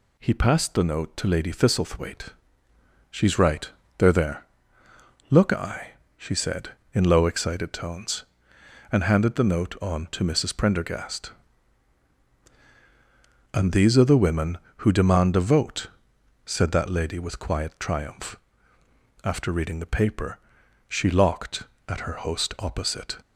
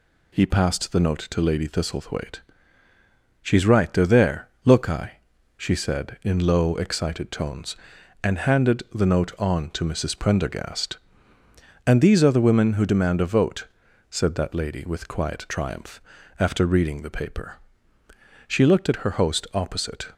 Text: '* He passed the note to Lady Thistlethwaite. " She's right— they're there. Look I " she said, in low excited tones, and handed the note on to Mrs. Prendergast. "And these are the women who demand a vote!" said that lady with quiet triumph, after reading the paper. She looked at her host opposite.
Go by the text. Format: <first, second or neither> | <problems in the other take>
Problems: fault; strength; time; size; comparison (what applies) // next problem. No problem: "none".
second | says "locked" for "looked"; at 21.1 s